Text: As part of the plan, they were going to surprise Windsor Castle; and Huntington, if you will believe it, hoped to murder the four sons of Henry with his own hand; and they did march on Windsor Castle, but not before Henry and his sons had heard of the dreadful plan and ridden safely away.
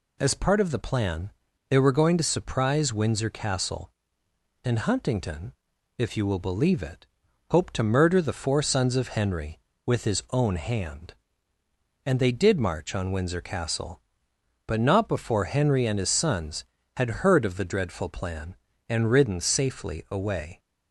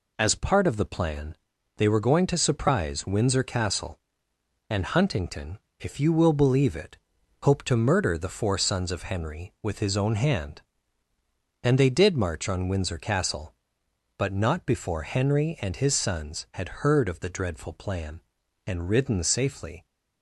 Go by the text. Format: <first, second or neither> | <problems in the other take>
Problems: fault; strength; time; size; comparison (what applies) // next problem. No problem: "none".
first | stops before "away"; at 19.8 s